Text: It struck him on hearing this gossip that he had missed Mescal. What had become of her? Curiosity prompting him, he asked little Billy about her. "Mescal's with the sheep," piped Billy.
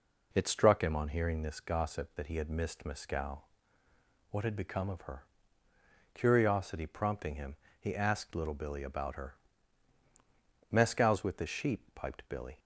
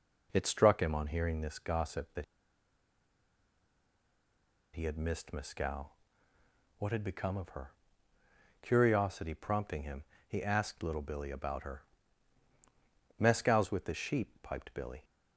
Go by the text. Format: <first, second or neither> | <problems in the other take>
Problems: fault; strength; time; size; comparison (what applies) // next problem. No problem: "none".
first | pauses between "that" and "he"; strong; at 2.2 s; 2.5 s long